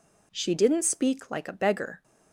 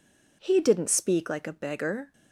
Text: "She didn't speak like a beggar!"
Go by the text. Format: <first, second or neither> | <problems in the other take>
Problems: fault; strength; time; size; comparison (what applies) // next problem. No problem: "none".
first | says "He" for "She"; at 0.4 s